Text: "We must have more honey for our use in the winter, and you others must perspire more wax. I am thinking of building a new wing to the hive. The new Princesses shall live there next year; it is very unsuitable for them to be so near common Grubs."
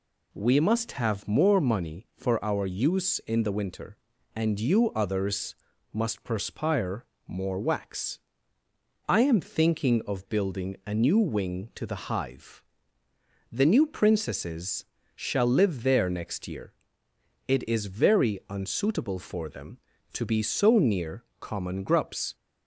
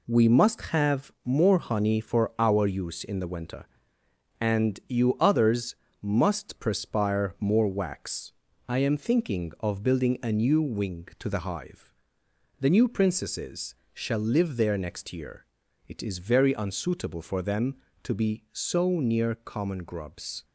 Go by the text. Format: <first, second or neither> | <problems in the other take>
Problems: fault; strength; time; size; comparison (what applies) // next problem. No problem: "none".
second | says "money" for "honey"; at 1.5 s // pauses between "others" and "must"; slight; at 5.5 s; 0.36 s long; slight in the second // pauses between "perspire" and "more"; slight; at 7.0 s; 0.22 s long // pauses between "Princesses" and "shall"; slight; at 14.8 s; 0.32 s long; slight in the second // pauses between "near" and "common"; slight; at 21.2 s; 0.16 s long